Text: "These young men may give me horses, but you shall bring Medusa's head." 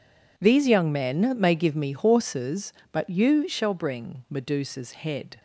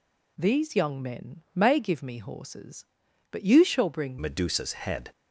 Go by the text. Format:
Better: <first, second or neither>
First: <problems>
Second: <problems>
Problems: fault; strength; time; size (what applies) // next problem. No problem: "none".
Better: first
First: none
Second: changes voice at "Medusa's"; from 4.2 s on; 0.9 s long